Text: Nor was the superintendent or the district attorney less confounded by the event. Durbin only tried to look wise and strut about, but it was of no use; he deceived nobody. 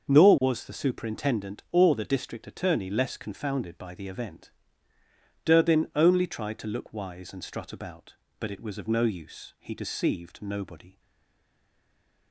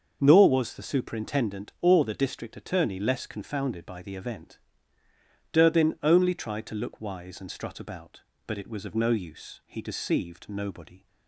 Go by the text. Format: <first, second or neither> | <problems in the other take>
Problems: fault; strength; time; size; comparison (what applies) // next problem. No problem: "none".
second | starts louder than the rest; until 1.1 s; 6.5 dB; also in the second // stays silent after the last word; noticeable; from 10.9 s on; 1.4 s long